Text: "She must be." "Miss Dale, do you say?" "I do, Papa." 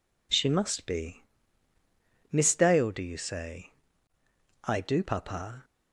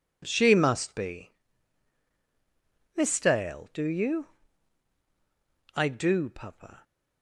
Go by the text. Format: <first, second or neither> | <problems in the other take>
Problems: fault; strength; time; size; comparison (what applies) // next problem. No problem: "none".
first | skips "say"; at 5.0 s